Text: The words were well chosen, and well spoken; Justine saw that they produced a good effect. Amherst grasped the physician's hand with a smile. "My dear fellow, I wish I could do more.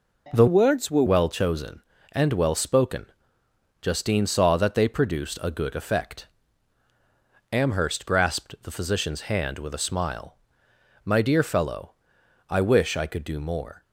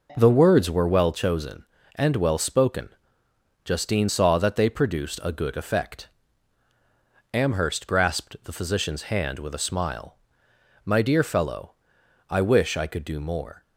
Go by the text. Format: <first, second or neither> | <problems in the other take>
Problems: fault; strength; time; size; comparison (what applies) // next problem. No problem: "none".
second | changes voice from "words" to "were"; from 0.4 to 1.0 s; 0.6 s long